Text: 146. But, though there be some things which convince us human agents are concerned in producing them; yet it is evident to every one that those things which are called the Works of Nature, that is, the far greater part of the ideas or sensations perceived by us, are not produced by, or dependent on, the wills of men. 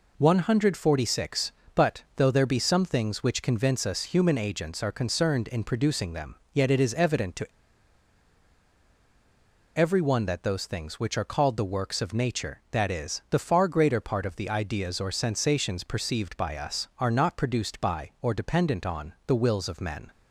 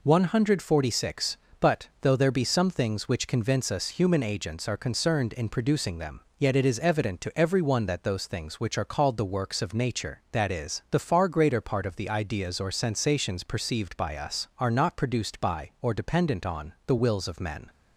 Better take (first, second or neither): second